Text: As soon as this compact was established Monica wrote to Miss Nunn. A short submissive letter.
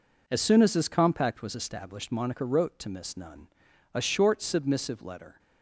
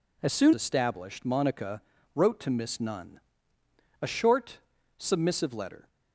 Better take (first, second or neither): first